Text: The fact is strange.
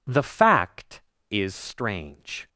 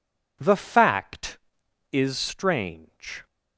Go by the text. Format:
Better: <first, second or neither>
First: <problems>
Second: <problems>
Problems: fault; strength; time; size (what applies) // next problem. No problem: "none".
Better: neither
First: none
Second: none